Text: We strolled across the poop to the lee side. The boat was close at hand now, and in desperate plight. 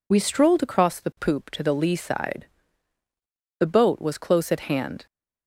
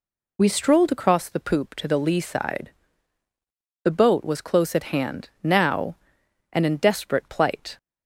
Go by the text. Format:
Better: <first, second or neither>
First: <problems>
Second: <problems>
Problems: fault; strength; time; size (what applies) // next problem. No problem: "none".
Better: second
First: stops before "now and in desperate plight"; at 5.0 s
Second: none